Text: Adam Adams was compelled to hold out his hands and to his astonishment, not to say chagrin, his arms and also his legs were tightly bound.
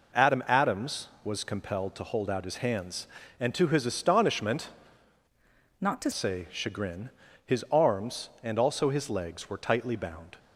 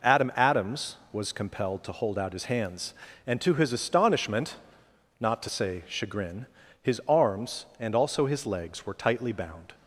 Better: second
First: changes voice from "not" to "to"; from 5.8 to 6.1 s; 0.3 s long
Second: none

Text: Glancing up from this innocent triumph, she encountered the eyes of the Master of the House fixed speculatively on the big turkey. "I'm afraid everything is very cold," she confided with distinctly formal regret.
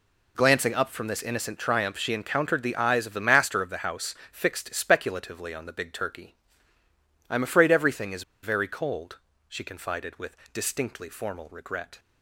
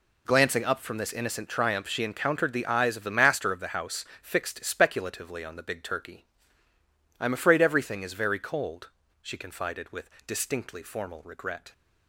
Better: second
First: pauses between "House" and "fixed"; slight; at 4.1 s; 0.16 s long // pauses between "is" and "very"; slight; at 8.2 s; 0.20 s long // pauses between "with" and "distinctly"; slight; at 10.3 s; 0.16 s long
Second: pauses between "House" and "fixed"; slight; at 4.0 s; 0.16 s long // pauses between "with" and "distinctly"; slight; at 10.1 s; 0.16 s long

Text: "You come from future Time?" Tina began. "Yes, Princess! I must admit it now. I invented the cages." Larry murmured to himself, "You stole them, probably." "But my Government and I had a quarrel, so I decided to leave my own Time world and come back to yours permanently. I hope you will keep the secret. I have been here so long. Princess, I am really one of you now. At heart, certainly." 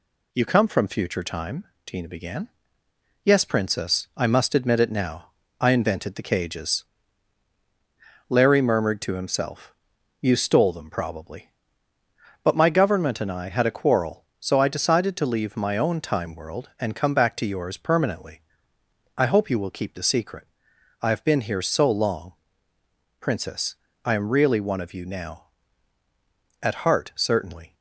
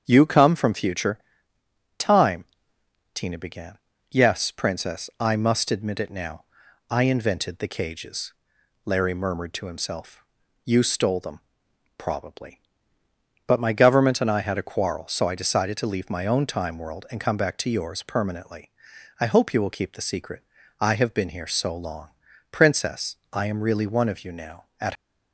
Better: first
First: none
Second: starts louder than the rest; strong; until 1.0 s; 7.5 dB // pauses between "future" and "Time"; noticeable; at 1.1 s; 0.80 s long // stops before "heart certainly"; at 24.9 s

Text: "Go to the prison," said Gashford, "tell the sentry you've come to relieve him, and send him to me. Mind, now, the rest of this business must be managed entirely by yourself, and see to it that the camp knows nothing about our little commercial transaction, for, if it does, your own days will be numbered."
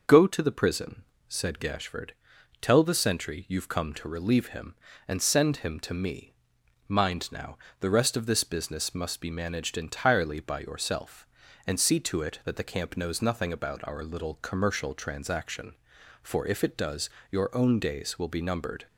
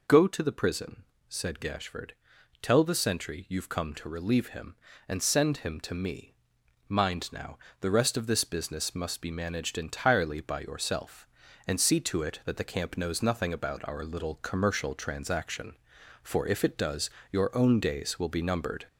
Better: first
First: none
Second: gets louder; slight; throughout; 2.5 dB

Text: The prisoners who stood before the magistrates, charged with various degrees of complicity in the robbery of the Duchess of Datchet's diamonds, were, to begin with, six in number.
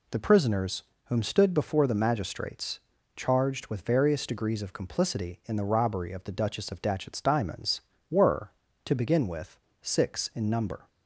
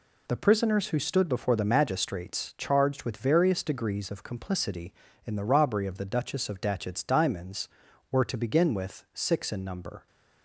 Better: second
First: says "whom" for "who"; at 1.0 s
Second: none

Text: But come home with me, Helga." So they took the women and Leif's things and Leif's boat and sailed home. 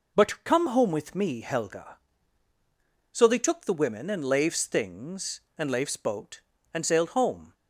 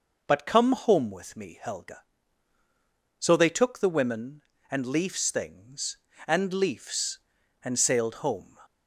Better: first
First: none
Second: skips "boat"; at 7.4 s

